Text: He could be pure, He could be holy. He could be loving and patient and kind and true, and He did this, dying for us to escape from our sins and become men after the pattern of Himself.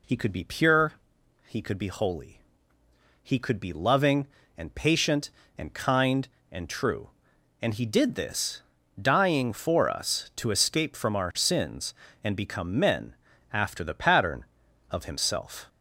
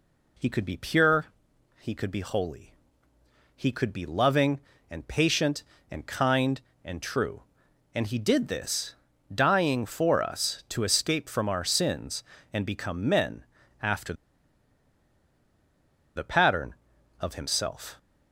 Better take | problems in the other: first | pauses between "men" and "after"; at 13.4 s; 0.38 s long; also in the first // pauses between "after" and "the"; strong; at 14.1 s; 2.0 s long

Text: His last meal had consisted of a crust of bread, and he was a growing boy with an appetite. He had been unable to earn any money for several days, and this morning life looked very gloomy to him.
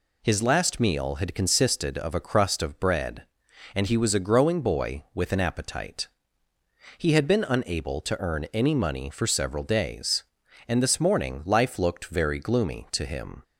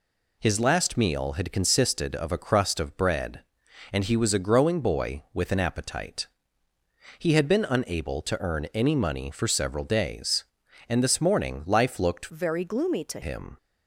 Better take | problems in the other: first | changes voice from "very" to "to"; from 12.3 to 13.2 s; 0.9 s long

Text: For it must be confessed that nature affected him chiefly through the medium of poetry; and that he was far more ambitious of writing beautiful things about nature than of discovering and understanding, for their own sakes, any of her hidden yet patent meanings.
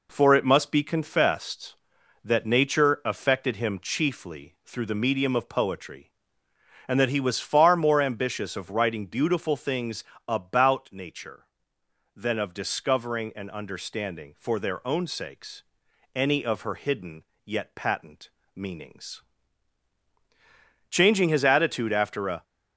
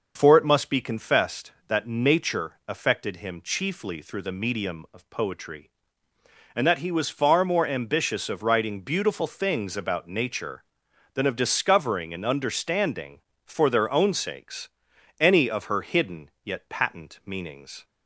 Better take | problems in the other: second | pauses between "things" and "about"; slight; at 10.0 s; 0.24 s long // pauses between "hidden" and "yet"; slight; at 17.2 s; 0.22 s long // pauses between "patent" and "meanings"; slight; at 18.3 s; 0.22 s long // goes on to say "Changing his attitude after a"; from 20.8 s on; 1.5 s long

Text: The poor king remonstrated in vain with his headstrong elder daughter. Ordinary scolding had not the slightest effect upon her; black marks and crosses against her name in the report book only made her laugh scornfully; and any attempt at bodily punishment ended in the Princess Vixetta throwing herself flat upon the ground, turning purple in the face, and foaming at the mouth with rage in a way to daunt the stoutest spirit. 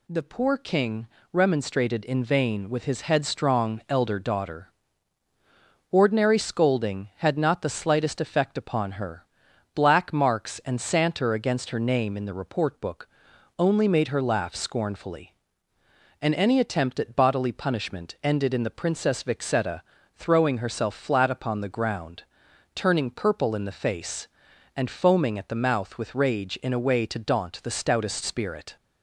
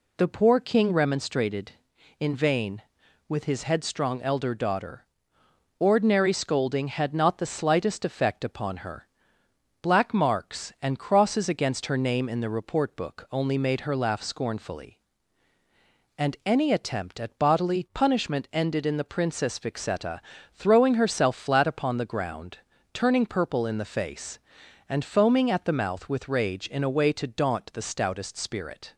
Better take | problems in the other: second | pauses between "king" and "remonstrated"; slight; at 1.0 s; 0.26 s long // says "santer" for "crosses"; at 10.7 s // pauses between "book" and "only"; noticeable; at 13.0 s; 0.52 s long // pauses between "Vixetta" and "throwing"; slight; at 19.8 s; 0.34 s long; slight in the second

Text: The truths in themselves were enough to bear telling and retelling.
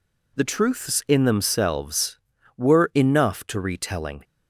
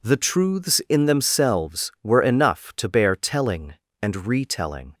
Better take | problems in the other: second | skips "bear telling and"; at 3.5 s

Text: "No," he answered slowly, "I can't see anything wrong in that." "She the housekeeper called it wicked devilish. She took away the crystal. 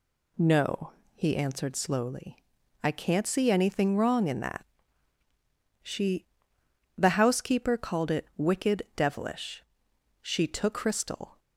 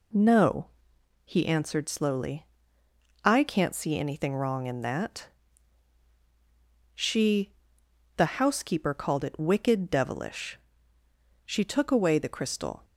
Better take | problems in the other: second | pauses between "She" and "the"; noticeable; at 6.2 s; 0.72 s long; noticeable in the second // skips "away the"; at 10.7 s

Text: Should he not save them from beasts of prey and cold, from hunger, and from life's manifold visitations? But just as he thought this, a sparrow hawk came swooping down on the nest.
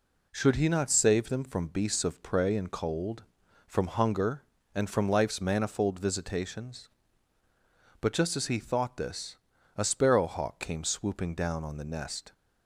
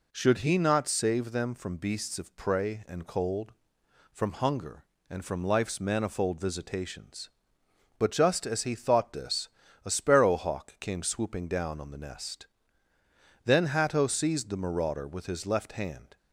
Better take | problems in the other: first | goes on to say "Then Hatto seized the marauder with his left hand"; strong; from 13.4 s on; 2.7 s long

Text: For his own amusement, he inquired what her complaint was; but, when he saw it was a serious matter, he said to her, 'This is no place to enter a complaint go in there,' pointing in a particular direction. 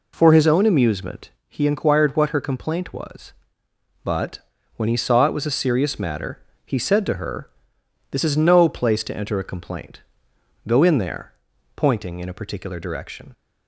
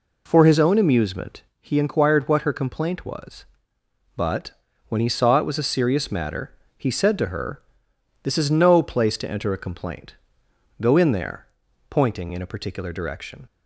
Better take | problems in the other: neither | pauses between "complaint" and "go"; noticeable; the same in both

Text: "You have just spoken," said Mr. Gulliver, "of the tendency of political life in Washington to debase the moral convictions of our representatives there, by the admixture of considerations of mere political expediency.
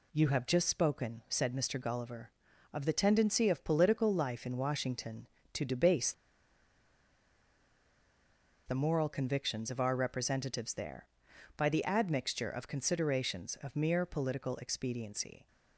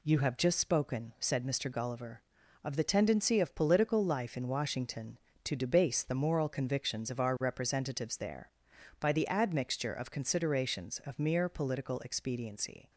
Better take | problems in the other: second | pauses between "debase" and "the"; strong; at 6.1 s; 2.5 s long

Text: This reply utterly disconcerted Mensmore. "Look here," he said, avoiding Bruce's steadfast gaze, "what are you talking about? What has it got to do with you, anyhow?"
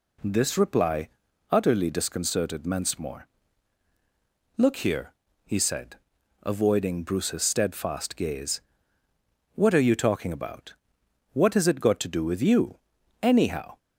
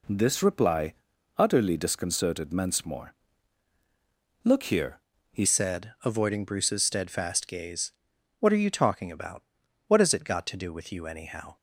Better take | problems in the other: first | pauses between "reply" and "utterly"; noticeable; at 0.9 s; 0.46 s long; also in the first // changes voice at "said"; from 5.4 s on; 6.1 s long

